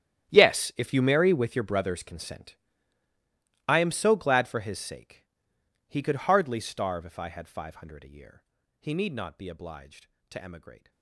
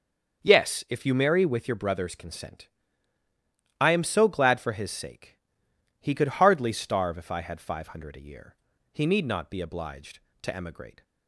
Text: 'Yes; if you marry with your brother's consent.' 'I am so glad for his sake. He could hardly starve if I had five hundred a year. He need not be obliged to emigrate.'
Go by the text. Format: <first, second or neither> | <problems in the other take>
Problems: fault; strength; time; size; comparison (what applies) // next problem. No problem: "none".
second | gets quieter; strong; throughout; 18 dB // starts louder than the rest; strong; until 1.3 s; 11 dB; also in the second